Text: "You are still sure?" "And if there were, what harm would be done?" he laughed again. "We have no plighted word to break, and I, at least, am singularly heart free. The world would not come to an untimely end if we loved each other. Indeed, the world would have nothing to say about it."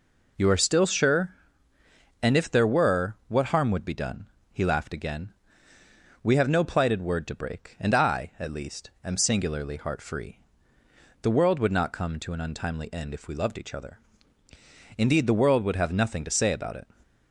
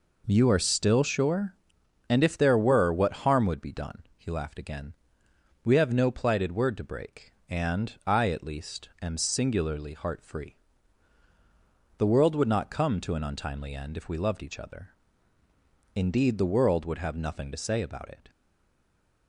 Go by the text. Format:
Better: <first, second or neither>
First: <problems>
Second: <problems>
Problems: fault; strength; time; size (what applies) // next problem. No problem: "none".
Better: first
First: none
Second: stays silent after the last word; from 18.2 s on; 1.0 s long